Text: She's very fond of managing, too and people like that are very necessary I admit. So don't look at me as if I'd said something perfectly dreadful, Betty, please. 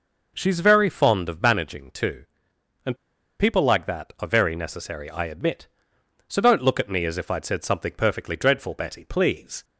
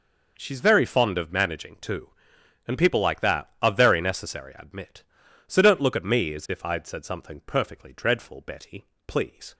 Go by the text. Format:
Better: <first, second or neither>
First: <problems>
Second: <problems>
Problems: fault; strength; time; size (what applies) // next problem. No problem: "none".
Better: second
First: pauses between "and" and "people"; at 2.9 s; 0.45 s long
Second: none